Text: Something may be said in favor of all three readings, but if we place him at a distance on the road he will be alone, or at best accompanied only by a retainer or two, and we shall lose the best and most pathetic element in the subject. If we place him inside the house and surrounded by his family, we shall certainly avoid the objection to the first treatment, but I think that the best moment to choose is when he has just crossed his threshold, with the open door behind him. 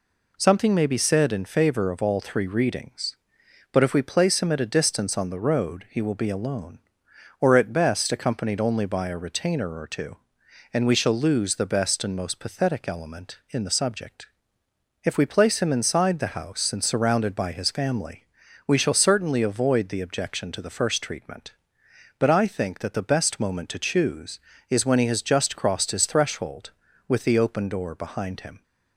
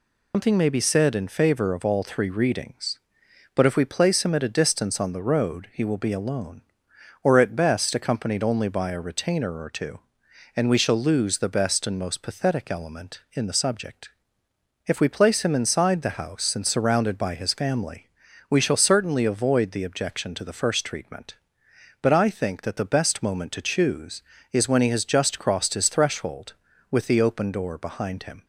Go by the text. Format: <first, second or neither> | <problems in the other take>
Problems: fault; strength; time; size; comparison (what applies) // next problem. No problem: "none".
first | loses the start of "Something"; at 0.3 s; 155 ms